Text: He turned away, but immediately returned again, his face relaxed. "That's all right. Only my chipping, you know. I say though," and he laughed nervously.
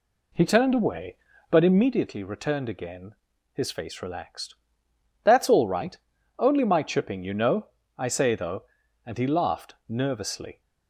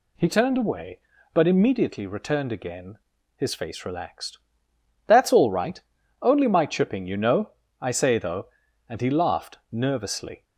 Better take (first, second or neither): second